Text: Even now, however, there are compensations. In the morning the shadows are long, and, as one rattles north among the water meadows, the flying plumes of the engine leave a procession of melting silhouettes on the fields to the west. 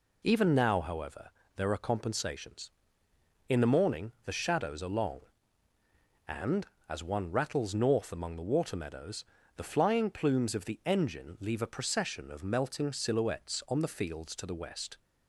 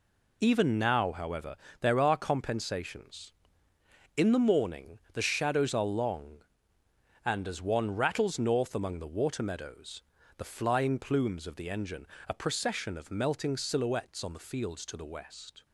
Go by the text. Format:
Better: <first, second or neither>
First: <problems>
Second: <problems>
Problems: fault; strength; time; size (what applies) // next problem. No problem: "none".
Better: first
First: none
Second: skips "leave"; at 12.1 s